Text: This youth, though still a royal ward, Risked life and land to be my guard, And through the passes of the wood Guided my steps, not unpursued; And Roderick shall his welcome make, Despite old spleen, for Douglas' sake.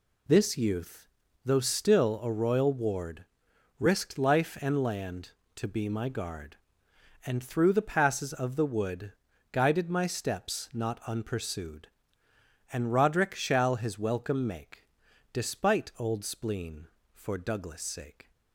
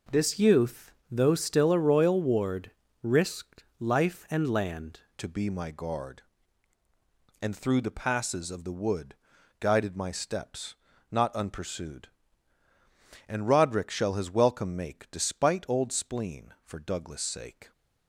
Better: first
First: pauses between "wood" and "Guided"; at 9.1 s; 0.40 s long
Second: pauses between "Risked" and "life"; slight; at 3.6 s; 0.16 s long // changes voice at "to"; from 5.1 s on; 12.6 s long // pauses between "wood" and "Guided"; noticeable; at 9.1 s; 0.46 s long

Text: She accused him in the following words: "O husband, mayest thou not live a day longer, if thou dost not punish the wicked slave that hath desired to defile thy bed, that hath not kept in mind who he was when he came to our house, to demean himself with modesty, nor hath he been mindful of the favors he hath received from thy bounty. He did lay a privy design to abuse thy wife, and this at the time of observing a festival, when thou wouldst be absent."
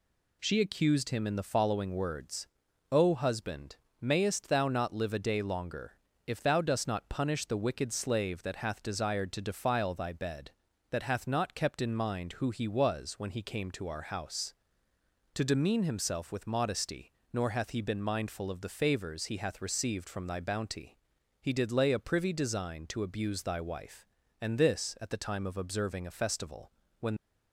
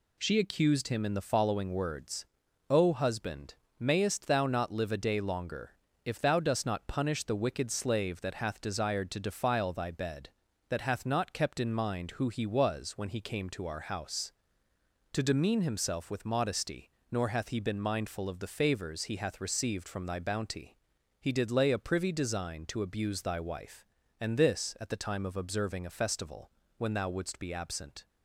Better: second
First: stops before "thou wouldst be absent"; at 27.1 s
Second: none

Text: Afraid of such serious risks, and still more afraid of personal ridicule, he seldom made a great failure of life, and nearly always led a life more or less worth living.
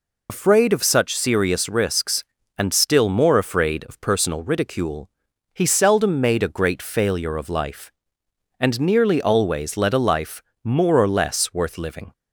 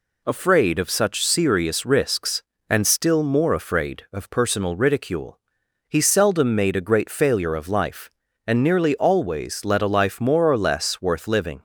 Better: second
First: loses the start of "Afraid"; at 0.2 s; 80 ms // pauses between "life" and "more"; slight; at 10.4 s; 0.20 s long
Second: none

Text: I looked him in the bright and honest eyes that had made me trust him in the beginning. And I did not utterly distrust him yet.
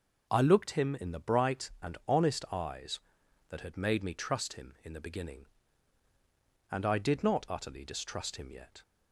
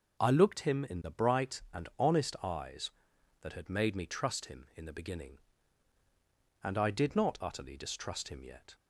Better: neither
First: none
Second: none

